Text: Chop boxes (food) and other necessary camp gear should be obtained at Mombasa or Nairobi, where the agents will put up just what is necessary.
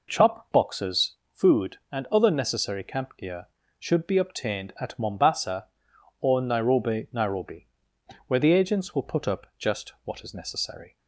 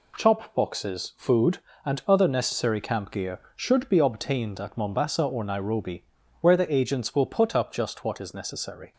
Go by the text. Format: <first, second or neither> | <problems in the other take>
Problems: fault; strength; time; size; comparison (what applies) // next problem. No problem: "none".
second | says "Nairobi" twice; at 7.1 s